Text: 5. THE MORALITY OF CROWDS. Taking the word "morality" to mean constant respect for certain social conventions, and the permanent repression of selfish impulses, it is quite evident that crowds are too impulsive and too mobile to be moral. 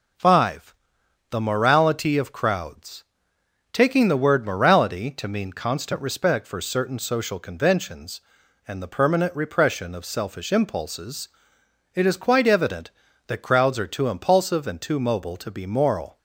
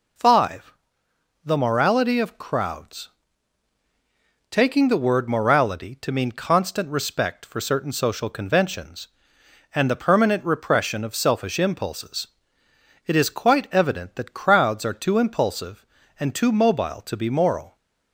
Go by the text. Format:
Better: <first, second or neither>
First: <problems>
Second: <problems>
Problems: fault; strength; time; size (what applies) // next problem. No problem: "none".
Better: neither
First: none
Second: none